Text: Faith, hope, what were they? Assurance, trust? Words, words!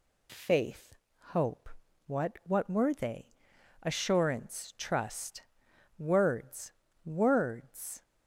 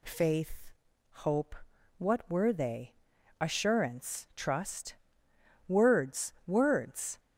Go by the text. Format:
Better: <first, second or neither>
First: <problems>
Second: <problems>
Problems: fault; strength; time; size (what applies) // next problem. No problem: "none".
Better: second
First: says "what" twice; at 2.4 s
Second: none